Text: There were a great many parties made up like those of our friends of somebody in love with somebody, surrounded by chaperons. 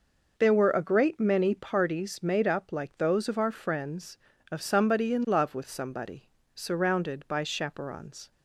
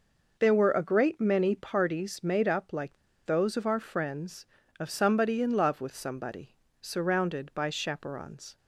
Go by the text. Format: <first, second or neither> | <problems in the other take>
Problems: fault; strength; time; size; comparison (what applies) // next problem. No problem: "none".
first | pauses between "like" and "those"; slight; at 2.9 s; 0.29 s long